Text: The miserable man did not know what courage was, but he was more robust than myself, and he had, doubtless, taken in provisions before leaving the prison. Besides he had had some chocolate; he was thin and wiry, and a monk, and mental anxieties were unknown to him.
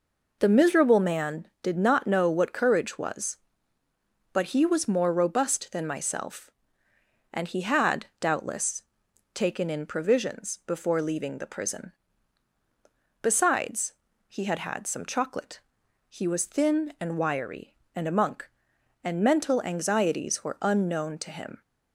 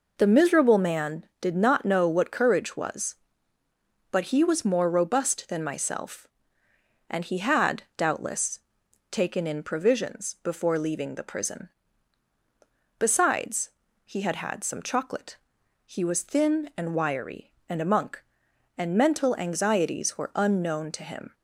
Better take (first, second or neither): neither